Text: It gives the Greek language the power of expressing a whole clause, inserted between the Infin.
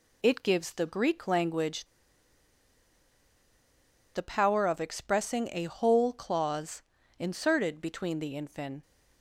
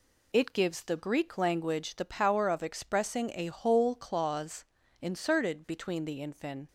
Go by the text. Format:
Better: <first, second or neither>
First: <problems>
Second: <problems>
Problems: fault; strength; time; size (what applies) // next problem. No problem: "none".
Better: second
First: pauses between "language" and "the"; strong; at 1.8 s; 2.2 s long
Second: none